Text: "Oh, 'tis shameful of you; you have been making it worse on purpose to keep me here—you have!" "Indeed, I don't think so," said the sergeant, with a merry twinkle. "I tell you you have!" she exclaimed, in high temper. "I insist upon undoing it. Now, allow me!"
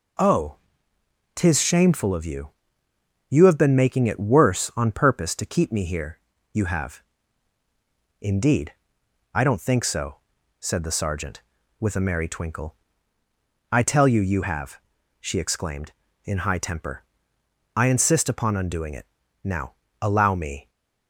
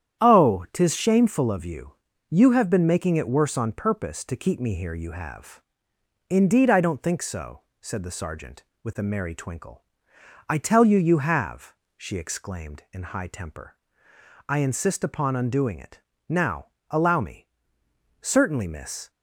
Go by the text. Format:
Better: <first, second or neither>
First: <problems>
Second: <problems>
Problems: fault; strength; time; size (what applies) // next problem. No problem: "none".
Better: first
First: none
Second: starts louder than the rest; strong; until 1.2 s; 9.5 dB // goes on to say "Certainly miss"; noticeable; from 18.2 s on; 0.88 s long